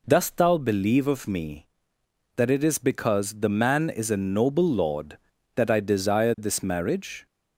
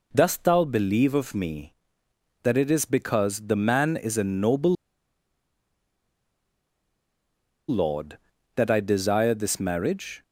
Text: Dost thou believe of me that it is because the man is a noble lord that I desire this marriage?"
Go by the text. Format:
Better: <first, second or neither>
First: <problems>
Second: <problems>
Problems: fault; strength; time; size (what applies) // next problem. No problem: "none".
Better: first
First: none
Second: pauses between "noble" and "lord"; strong; at 4.7 s; 2.9 s long